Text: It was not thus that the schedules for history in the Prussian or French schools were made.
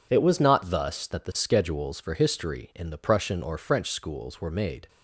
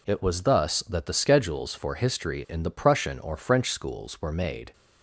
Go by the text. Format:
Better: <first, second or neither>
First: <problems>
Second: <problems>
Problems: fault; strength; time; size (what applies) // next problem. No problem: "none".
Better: first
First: none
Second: skips "not"; at 0.4 s